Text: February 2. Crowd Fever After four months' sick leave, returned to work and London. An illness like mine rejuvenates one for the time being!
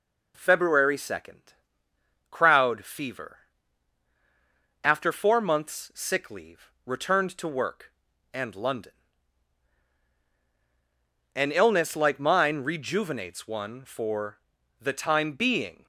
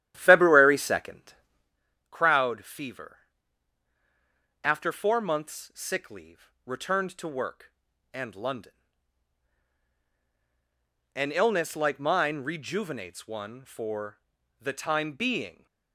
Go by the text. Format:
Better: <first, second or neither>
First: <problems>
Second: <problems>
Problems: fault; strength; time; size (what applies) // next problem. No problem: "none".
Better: first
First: pauses between "Fever" and "After"; strong; at 3.3 s; 1.4 s long // pauses between "for" and "the"; at 14.3 s; 0.42 s long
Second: starts louder than the rest; strong; until 1.8 s; 12 dB // pauses between "Fever" and "After"; strong; at 3.1 s; 1.4 s long // pauses between "for" and "the"; at 14.1 s; 0.42 s long